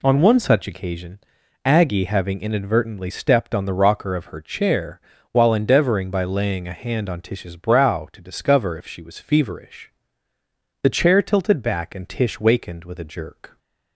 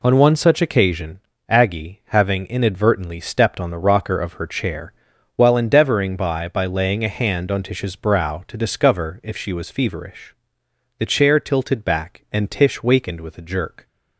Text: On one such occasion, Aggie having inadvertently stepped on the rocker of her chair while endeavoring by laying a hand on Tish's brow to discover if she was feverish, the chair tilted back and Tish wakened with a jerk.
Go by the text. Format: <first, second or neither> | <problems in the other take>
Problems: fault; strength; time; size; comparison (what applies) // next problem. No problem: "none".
first | pauses between "chair" and "while"; at 4.9 s; 0.44 s long; slight in the first // says "by" twice; at 6.4 s